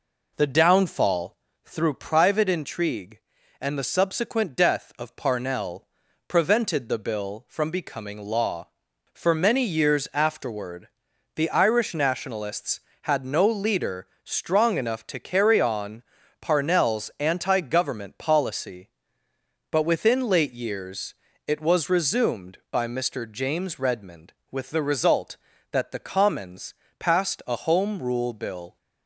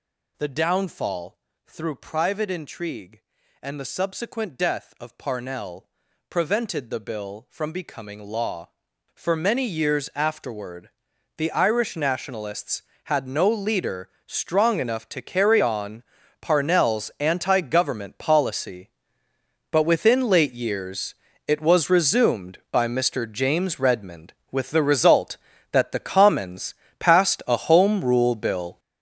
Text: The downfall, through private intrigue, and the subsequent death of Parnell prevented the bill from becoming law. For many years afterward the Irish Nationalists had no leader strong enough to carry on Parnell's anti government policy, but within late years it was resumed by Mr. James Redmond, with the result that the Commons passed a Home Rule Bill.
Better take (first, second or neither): first